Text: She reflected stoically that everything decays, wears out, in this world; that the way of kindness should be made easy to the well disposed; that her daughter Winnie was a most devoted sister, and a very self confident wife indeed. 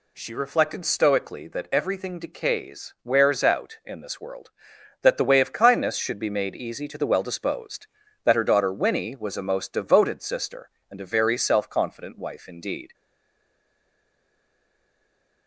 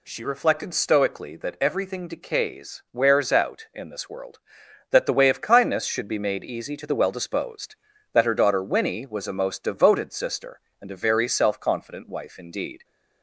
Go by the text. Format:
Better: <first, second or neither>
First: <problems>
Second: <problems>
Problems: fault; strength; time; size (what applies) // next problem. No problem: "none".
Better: second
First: stays silent after the last word; strong; from 12.9 s on; 2.5 s long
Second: none